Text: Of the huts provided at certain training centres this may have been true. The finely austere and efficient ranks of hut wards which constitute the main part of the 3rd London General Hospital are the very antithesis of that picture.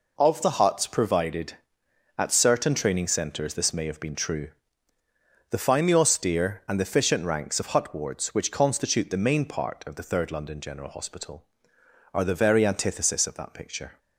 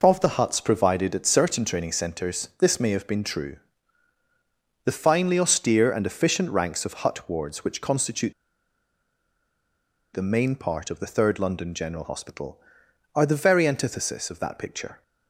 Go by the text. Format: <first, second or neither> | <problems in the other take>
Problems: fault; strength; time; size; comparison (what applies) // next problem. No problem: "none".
first | pauses between "constitute" and "the"; strong; at 8.3 s; 1.8 s long